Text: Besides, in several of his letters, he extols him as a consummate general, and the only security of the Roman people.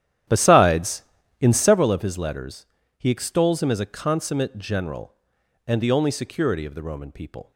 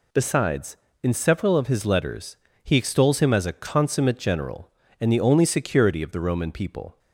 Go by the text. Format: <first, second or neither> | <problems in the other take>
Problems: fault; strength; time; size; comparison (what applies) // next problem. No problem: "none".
second | starts louder than the rest; strong; until 1.8 s; 11 dB